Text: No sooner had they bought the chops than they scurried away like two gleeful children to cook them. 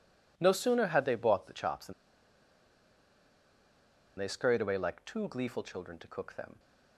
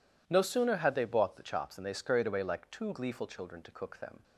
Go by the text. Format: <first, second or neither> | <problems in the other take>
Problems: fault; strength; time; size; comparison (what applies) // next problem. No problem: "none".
second | pauses between "than" and "they"; strong; at 1.9 s; 2.2 s long